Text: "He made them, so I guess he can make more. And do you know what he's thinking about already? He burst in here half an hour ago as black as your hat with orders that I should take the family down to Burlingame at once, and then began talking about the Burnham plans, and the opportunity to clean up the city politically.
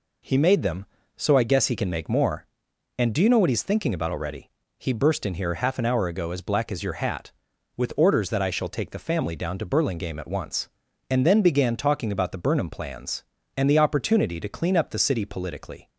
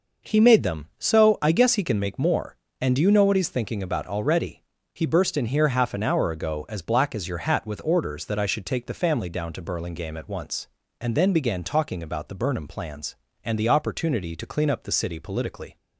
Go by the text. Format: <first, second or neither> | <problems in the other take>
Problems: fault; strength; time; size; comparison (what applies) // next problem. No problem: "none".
second | says "shall" for "should"; at 8.4 s